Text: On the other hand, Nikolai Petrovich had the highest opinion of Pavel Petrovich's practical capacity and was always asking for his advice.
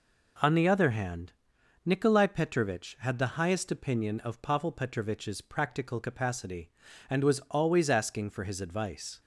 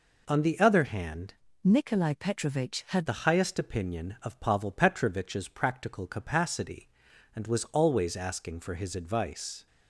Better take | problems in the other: first | changes voice from "Nikolai" to "had"; from 1.6 to 3.0 s; 1.4 s long

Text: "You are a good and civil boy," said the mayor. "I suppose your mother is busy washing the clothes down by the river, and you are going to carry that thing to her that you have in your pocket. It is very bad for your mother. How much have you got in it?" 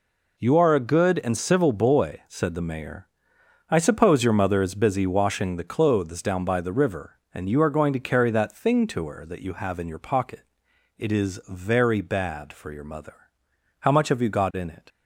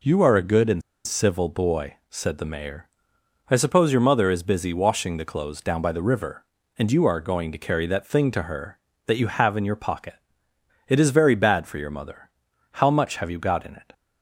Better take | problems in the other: first | pauses between "and" and "civil"; slight; at 0.8 s; 0.25 s long

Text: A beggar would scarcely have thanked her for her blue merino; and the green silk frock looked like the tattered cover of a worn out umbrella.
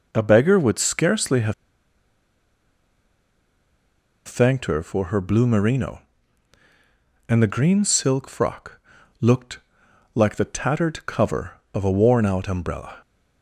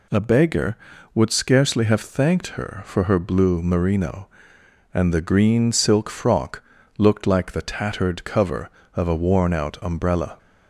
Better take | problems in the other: second | pauses between "have" and "thanked"; strong; at 1.5 s; 2.7 s long // pauses between "frock" and "looked"; at 8.8 s; 0.40 s long; slight in the second // pauses between "looked" and "like"; noticeable; at 9.5 s; 0.56 s long

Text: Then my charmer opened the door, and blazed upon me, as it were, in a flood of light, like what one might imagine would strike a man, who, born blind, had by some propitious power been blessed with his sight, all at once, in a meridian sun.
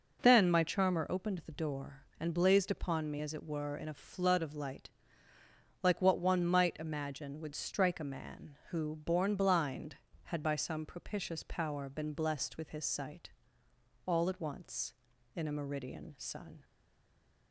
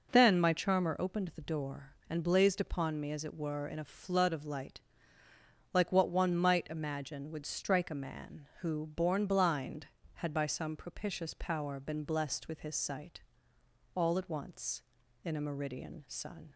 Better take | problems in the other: second | stays silent after the last word; slight; from 16.6 s on; 0.9 s long

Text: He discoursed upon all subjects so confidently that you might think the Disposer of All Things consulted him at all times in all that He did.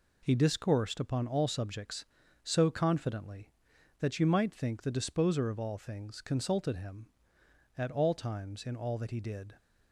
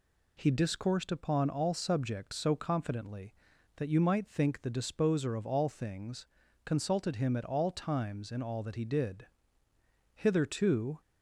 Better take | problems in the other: first | pauses between "Things" and "consulted"; at 6.2 s; 0.38 s long // goes on to say "Hitherto"; noticeable; from 10.1 s on; 0.86 s long

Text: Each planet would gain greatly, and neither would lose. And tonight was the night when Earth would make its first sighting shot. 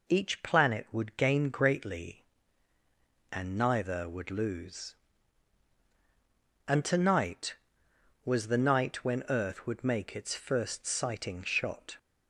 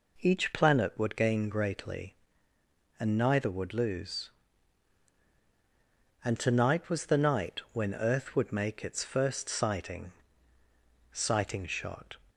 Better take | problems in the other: first | says "sighting" twice; at 11.1 s

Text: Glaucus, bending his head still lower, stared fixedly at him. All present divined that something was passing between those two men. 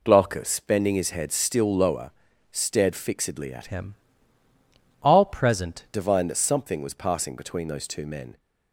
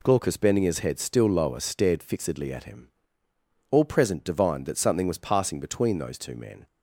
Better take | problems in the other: second | changes voice from "him" to "present"; from 3.6 to 5.8 s; 2.2 s long

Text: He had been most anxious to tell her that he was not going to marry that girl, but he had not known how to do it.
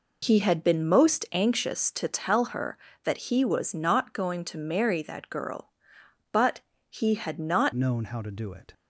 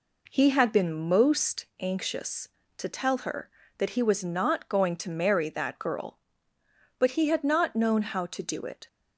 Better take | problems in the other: second | pauses between "but" and "he"; slight; at 6.6 s; 0.26 s long // changes voice at "known"; from 7.7 s on; 1.0 s long

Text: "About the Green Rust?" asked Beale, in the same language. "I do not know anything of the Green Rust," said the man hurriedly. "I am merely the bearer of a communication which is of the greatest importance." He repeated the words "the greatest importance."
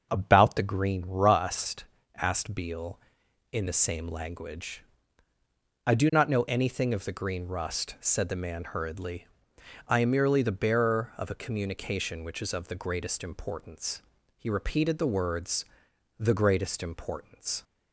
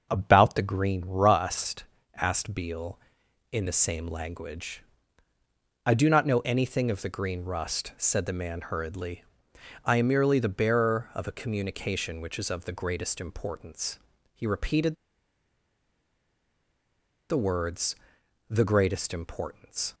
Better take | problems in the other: first | starts louder than the rest; until 1.1 s; 6.5 dB; also in the first // pauses between "repeated" and "the"; strong; at 14.9 s; 2.3 s long // pauses between "words" and "the"; noticeable; at 17.9 s; 0.56 s long; noticeable in the first

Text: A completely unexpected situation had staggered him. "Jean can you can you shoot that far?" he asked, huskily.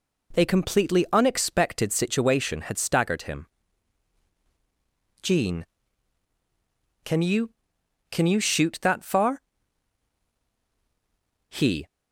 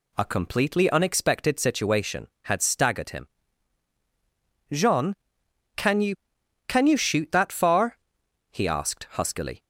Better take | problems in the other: second | stops before "asked huskily"; at 11.8 s

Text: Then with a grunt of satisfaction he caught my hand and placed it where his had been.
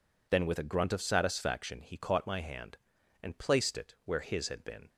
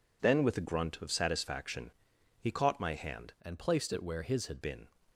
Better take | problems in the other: first | pauses between "satisfaction" and "he"; noticeable; at 1.9 s; 0.50 s long // changes voice from "and" to "had"; from 3.4 to 4.6 s; 1.2 s long

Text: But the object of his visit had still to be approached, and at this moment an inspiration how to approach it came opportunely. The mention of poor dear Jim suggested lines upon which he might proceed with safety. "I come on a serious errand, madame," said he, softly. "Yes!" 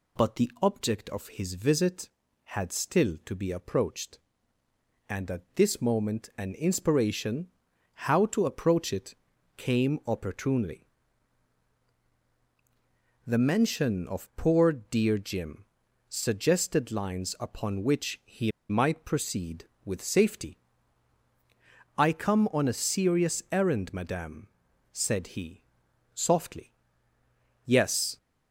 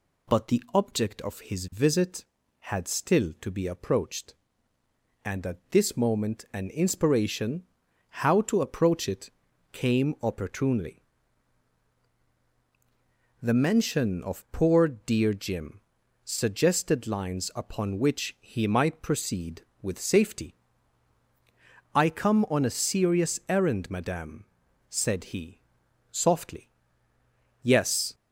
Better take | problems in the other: second | pauses between "inspiration" and "how"; noticeable; at 7.4 s; 0.52 s long; noticeable in the second // pauses between "it" and "came"; at 9.1 s; 0.42 s long; also in the second // pauses between "Jim" and "suggested"; at 15.6 s; 0.44 s long; also in the second // pauses between "he" and "might"; slight; at 18.5 s; 0.18 s long

